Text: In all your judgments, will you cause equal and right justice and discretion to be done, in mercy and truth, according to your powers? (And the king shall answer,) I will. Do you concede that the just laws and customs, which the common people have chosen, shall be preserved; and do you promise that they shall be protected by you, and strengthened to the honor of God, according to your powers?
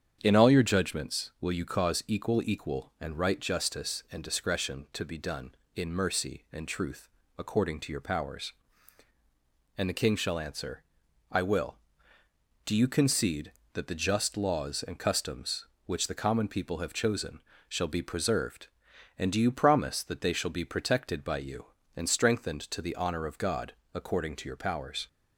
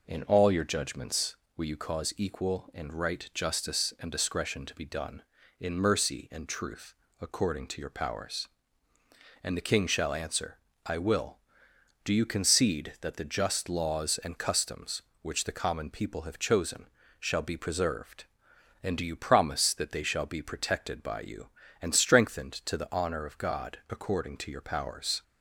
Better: second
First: starts louder than the rest; strong; until 1.2 s; 8 dB // says "equal" twice; at 2.4 s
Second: none

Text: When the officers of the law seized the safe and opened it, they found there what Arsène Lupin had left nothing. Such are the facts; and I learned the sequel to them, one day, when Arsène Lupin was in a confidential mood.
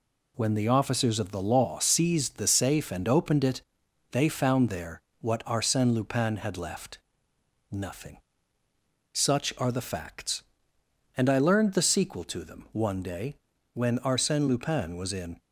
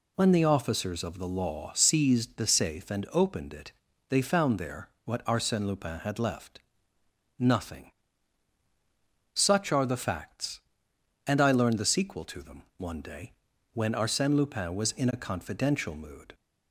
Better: second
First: pauses between "there" and "what"; slight; at 5.0 s; 0.20 s long // pauses between "left" and "nothing"; noticeable; at 6.9 s; 0.74 s long // stops before "a confidential mood"; at 15.3 s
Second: pauses between "there" and "what"; slight; at 4.8 s; 0.16 s long // pauses between "left" and "nothing"; noticeable; at 6.5 s; 0.78 s long

